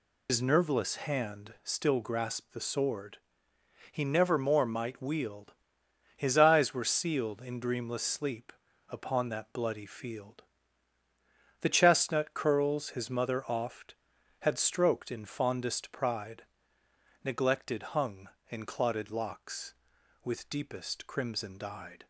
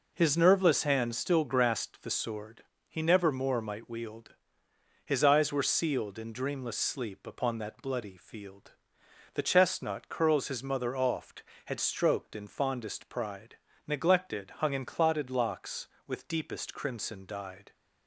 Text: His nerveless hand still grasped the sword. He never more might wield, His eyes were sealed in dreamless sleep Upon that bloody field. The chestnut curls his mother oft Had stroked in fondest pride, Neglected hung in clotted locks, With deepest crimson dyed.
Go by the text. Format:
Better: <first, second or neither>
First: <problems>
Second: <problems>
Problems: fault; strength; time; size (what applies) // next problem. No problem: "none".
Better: second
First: loses the start of "His"; at 0.2 s; 95 ms // pauses between "sleep" and "Upon"; at 8.5 s; 0.38 s long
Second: none